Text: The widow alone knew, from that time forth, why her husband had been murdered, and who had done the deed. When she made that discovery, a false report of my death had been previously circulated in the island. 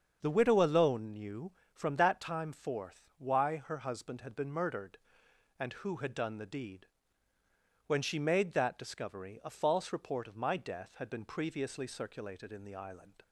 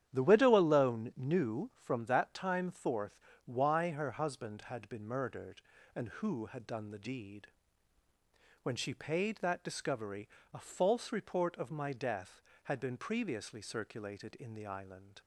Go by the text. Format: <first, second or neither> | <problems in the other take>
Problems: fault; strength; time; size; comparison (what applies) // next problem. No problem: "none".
first | starts louder than the rest; strong; until 1.1 s; 10 dB; also in the first // says "paid" for "made"; at 8.9 s